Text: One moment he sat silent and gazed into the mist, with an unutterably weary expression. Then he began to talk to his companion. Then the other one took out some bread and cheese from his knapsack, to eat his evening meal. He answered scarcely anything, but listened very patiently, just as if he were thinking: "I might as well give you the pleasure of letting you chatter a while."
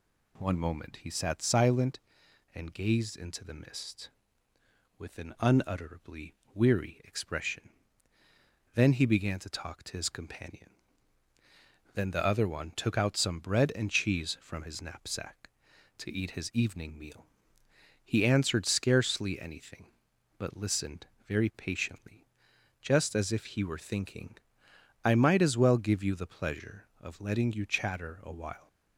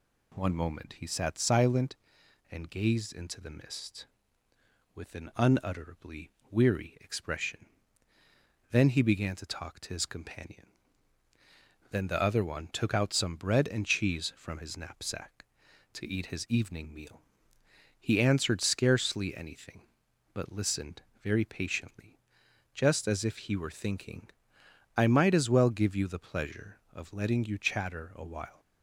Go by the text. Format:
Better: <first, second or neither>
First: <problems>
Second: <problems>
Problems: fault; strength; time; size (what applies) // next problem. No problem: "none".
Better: neither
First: pauses between "unutterably" and "weary"; slight; at 6.3 s; 0.20 s long // pauses between "listened" and "very"; slight; at 21.0 s; 0.20 s long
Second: pauses between "unutterably" and "weary"; slight; at 6.3 s; 0.20 s long // pauses between "listened" and "very"; slight; at 21.0 s; 0.20 s long